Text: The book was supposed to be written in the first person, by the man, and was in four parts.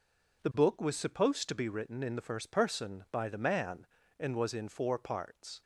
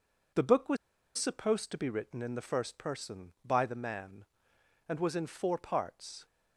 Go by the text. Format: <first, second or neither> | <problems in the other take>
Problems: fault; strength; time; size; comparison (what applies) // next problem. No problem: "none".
first | pauses between "was" and "supposed"; at 0.7 s; 0.40 s long